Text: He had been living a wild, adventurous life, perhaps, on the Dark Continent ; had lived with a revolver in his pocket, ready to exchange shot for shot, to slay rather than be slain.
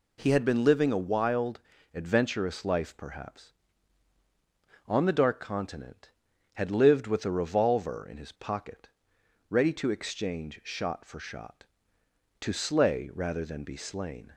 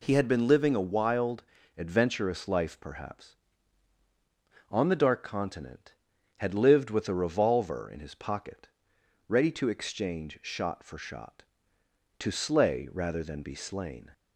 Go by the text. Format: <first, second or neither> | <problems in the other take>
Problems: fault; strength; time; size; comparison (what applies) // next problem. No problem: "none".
neither | none